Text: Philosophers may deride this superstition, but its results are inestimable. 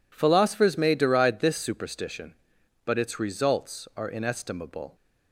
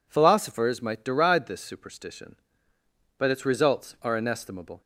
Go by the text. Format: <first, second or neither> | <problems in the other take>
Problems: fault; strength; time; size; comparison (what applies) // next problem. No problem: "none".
first | says "might" for "may"; at 0.8 s